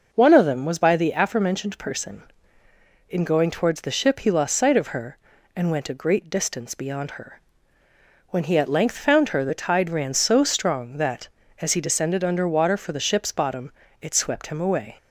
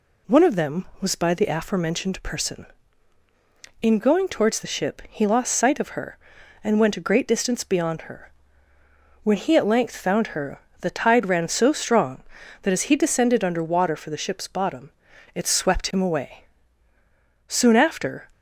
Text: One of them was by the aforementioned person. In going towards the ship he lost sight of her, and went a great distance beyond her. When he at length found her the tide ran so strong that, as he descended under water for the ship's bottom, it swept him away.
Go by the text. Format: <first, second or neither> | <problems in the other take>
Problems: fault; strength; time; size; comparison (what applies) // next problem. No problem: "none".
first | pauses between "her" and "the"; slight; at 10.6 s; 0.22 s long // goes on to say "Soon after"; noticeable; from 17.4 s on; 0.80 s long